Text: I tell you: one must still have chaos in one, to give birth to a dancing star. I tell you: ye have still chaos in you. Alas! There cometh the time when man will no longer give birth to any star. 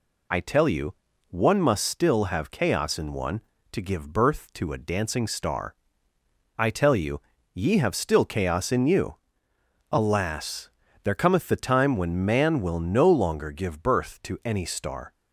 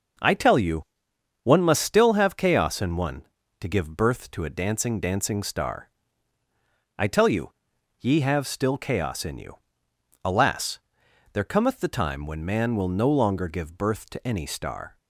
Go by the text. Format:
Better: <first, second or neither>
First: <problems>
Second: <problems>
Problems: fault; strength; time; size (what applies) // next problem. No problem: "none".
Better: first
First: none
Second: starts louder than the rest; noticeable; until 1.7 s; 6 dB // says "dancing" twice; at 4.9 s